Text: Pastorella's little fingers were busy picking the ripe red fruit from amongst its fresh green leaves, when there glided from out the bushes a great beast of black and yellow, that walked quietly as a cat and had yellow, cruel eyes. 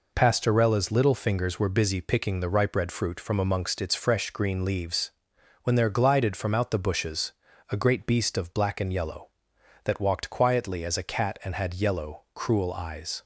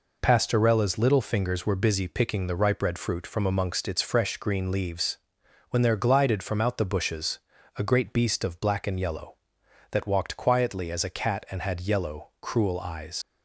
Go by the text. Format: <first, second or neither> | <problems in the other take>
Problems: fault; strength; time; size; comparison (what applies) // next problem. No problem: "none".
first | pauses between "bushes" and "a"; at 7.3 s; 0.38 s long; also in the first // leaves "eyes" unfinished; at 13.2 s; 85 ms